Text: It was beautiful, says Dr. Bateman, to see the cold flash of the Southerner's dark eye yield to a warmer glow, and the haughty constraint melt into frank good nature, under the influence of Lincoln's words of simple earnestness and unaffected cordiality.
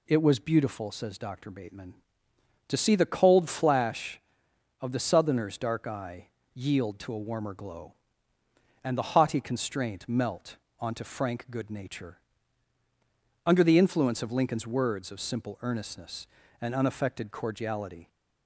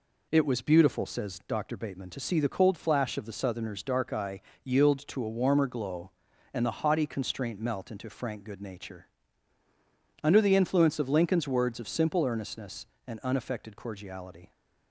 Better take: second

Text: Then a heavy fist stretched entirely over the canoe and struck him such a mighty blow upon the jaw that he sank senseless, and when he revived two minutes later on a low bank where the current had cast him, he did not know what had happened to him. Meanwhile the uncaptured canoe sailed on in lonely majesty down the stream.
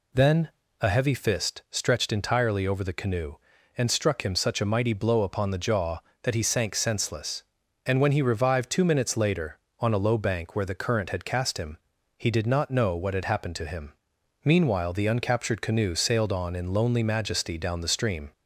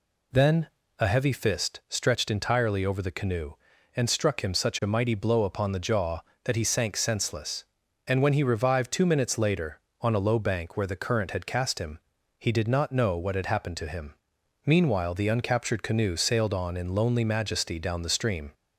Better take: neither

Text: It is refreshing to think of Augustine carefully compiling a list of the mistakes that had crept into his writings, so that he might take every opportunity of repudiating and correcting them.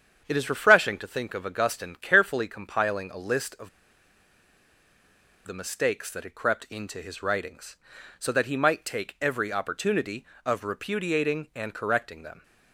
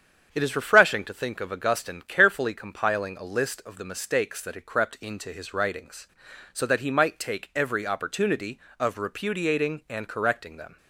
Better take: second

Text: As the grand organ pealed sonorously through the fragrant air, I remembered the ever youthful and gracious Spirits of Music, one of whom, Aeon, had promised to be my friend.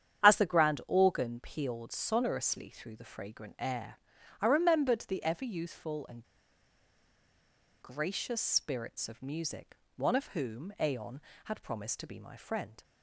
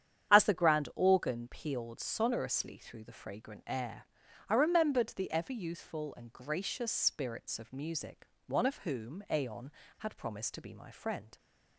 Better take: second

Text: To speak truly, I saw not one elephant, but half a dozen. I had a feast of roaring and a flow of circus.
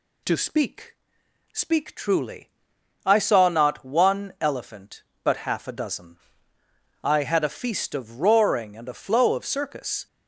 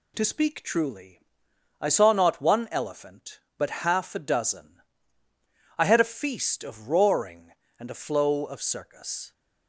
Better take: second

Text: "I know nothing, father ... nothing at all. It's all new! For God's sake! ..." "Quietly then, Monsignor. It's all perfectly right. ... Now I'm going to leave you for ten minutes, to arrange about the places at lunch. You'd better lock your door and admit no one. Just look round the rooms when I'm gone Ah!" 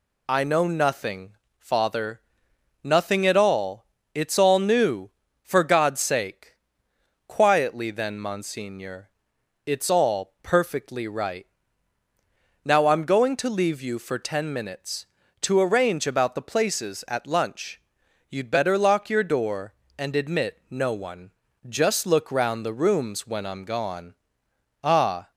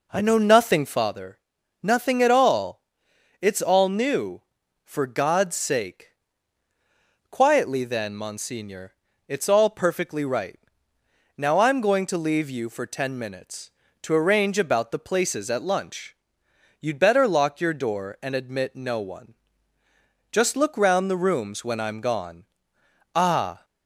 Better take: first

